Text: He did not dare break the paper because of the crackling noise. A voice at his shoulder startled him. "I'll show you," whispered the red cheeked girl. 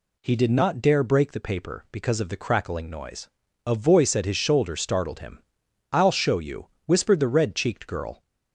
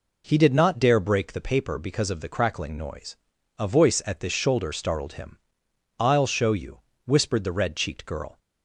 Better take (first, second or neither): first